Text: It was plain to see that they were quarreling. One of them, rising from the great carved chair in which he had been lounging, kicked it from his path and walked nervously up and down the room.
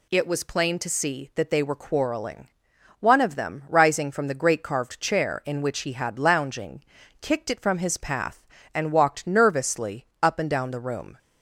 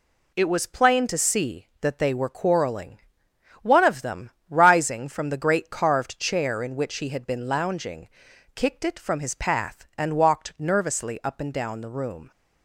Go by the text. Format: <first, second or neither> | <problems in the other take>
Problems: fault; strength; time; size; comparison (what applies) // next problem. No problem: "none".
second | skips "been"; at 6.1 s // pauses between "nervously" and "up"; slight; at 10.0 s; 0.16 s long